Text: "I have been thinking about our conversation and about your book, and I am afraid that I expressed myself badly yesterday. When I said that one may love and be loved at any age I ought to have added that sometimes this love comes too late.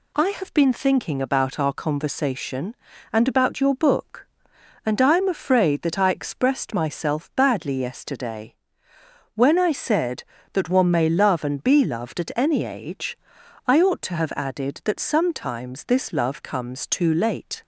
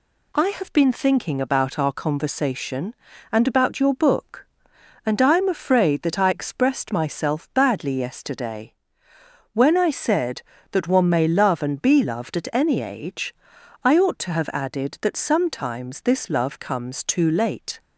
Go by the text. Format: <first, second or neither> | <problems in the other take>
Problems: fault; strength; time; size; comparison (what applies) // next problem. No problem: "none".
neither | pauses between "age" and "I"; noticeable; the same in both